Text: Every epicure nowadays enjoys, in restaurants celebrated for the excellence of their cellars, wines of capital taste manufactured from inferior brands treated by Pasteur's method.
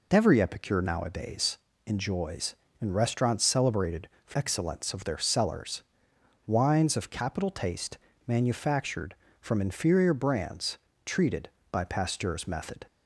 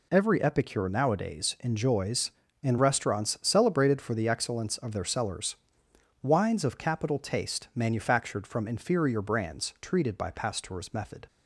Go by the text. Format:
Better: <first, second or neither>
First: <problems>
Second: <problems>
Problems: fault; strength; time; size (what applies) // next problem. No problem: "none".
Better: second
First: pauses between "nowadays" and "enjoys"; slight; at 1.5 s; 0.26 s long // skips "the"; at 4.3 s // pauses between "taste" and "manufactured"; slight; at 7.9 s; 0.28 s long // pauses between "brands" and "treated"; slight; at 10.7 s; 0.28 s long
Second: none